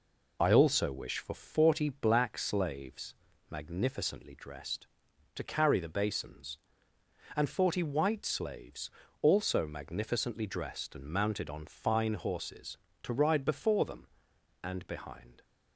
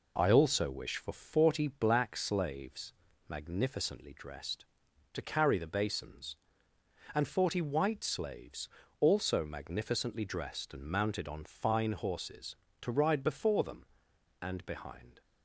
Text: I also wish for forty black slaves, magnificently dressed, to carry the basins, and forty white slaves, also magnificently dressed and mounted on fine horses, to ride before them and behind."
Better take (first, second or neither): second